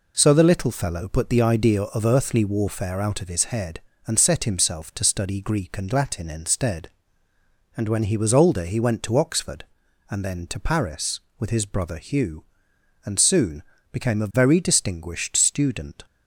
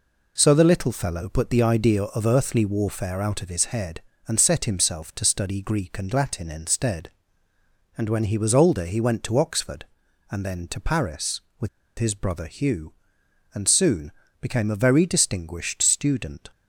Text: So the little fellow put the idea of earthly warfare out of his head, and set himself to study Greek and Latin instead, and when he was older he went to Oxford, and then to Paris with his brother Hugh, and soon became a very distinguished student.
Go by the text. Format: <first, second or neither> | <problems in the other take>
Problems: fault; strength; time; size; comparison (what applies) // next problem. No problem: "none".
first | pauses between "with" and "his"; slight; at 11.6 s; 0.29 s long // pauses between "soon" and "became"; slight; at 14.1 s; 0.30 s long; slight in the first